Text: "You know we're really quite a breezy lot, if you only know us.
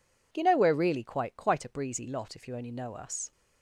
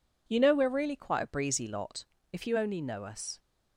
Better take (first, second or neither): second